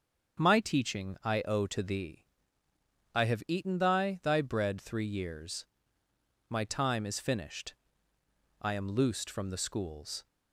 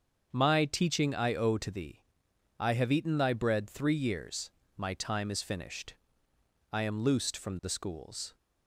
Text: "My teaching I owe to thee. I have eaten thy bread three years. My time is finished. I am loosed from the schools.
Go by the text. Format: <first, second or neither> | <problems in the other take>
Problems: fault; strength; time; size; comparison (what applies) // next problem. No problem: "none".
second | starts louder than the rest; strong; until 1.5 s; 7 dB; also in the second // says "thy" twice; at 4.2 s